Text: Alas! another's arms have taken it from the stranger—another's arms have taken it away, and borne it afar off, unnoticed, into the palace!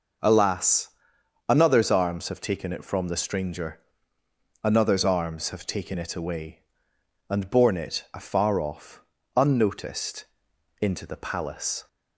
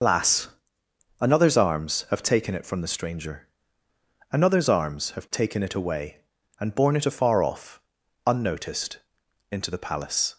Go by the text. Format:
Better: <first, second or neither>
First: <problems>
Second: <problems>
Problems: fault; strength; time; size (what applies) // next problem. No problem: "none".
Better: first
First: none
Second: loses the start of "Alas"; at 0.0 s; 125 ms